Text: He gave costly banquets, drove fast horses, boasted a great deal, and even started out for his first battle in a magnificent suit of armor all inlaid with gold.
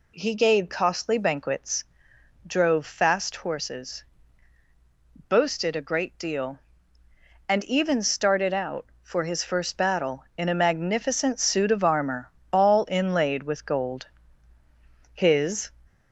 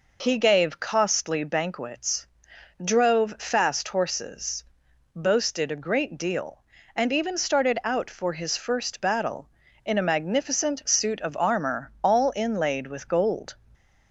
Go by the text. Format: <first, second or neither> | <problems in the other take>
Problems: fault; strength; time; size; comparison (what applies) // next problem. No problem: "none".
second | pauses between "armor" and "all"; slight; at 12.2 s; 0.22 s long // goes on to say "His"; from 15.1 s on; 0.56 s long